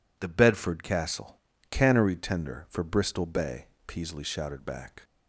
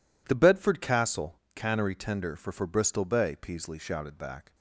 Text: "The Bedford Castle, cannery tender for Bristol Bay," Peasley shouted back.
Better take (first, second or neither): first